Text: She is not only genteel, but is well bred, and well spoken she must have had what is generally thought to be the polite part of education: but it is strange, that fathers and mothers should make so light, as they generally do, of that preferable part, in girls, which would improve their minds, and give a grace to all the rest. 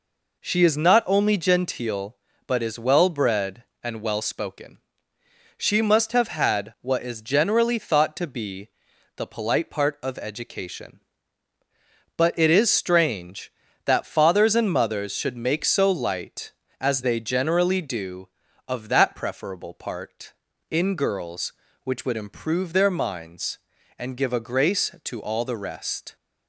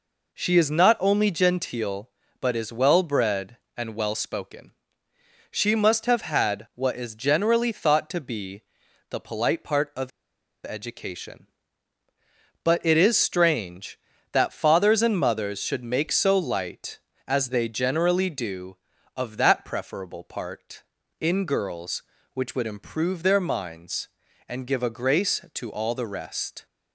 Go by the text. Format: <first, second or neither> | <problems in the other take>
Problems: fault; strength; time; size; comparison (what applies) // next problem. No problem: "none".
first | pauses between "spoken" and "she"; noticeable; at 4.7 s; 0.78 s long; noticeable in the first // pauses between "be" and "the"; noticeable; at 8.5 s; 0.48 s long; noticeable in the first // pauses between "of" and "education"; noticeable; at 10.1 s; 0.55 s long